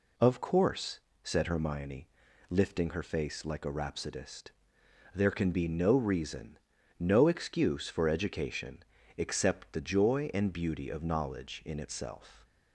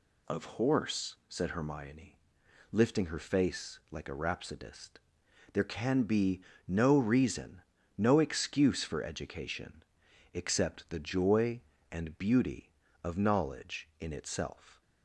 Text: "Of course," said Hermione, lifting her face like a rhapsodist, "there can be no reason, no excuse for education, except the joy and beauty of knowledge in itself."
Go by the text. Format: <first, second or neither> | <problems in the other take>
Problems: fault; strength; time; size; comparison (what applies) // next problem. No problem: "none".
first | says "horse" for "course"; at 0.5 s // pauses between "be" and "no"; slight; at 6.4 s; 0.26 s long